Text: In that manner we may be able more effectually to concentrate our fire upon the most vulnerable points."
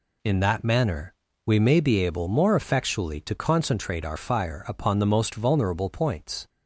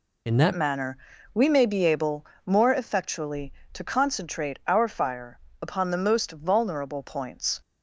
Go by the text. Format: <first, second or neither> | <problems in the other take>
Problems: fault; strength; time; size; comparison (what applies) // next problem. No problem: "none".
first | changes voice at "manner"; from 0.5 s on; 7.0 s long // pauses between "manner" and "we"; at 0.9 s; 0.38 s long; slight in the first // pauses between "able" and "more"; slight; at 2.2 s; 0.20 s long // pauses between "fire" and "upon"; slight; at 5.3 s; 0.24 s long